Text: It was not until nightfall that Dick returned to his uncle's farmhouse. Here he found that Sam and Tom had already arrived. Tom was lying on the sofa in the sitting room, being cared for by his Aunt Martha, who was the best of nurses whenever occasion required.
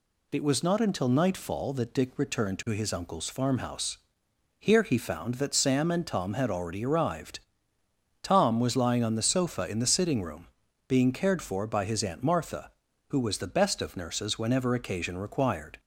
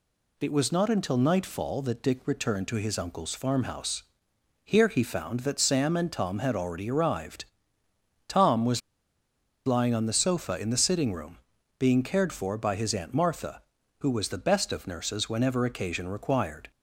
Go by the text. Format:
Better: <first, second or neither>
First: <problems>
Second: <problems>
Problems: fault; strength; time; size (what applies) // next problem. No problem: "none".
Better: first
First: none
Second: pauses between "was" and "lying"; noticeable; at 8.8 s; 0.85 s long